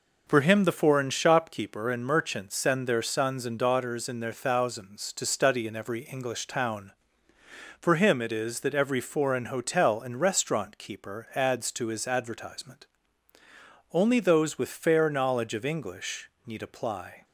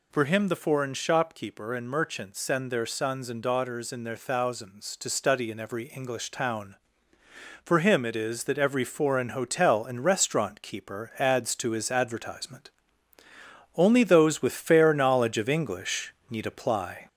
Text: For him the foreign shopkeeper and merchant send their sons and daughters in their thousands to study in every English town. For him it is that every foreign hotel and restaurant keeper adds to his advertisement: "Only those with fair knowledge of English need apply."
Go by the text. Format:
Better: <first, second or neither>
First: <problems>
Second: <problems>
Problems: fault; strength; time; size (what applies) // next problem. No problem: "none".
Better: first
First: pauses between "English" and "need"; slight; at 16.2 s; 0.18 s long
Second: gets louder; slight; throughout; 3 dB // pauses between "English" and "need"; slight; at 16.1 s; 0.18 s long